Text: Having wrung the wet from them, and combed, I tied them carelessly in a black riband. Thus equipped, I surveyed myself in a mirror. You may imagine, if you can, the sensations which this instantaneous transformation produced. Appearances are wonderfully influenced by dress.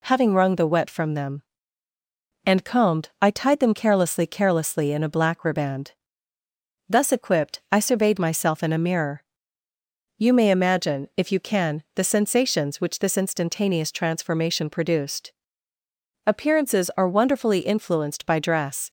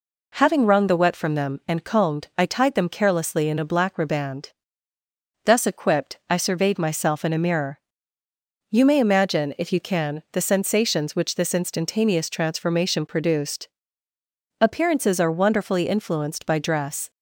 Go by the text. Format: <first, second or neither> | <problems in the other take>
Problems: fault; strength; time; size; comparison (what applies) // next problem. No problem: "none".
second | says "carelessly" twice; at 4.2 s